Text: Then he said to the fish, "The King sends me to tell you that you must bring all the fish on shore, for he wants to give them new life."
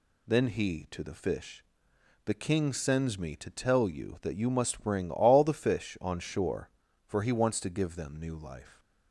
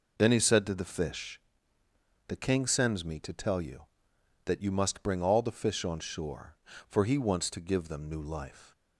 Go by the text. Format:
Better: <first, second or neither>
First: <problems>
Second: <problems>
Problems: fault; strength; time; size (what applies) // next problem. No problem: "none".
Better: second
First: skips "said"; at 0.8 s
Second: none